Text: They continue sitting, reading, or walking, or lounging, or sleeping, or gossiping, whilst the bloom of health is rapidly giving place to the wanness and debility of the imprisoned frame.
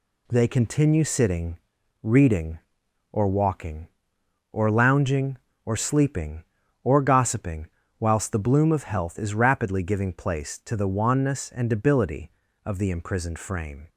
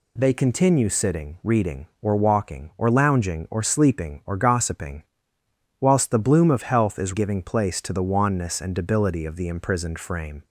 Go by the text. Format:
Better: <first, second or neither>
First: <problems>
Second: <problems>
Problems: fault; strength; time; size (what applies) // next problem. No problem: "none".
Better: first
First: none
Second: skips "rapidly"; at 7.1 s